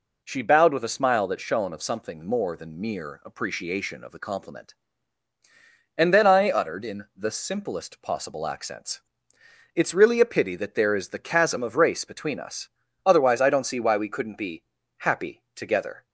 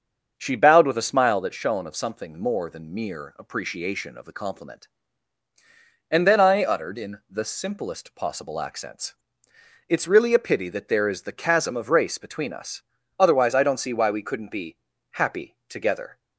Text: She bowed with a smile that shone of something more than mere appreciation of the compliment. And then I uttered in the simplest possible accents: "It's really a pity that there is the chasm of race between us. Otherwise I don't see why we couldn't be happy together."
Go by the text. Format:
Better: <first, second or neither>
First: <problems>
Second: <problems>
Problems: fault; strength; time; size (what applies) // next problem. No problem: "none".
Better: first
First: pauses between "be" and "happy"; slight; at 14.6 s; 0.36 s long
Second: starts louder than the rest; until 1.4 s; 6.5 dB // pauses between "be" and "happy"; slight; at 14.7 s; 0.36 s long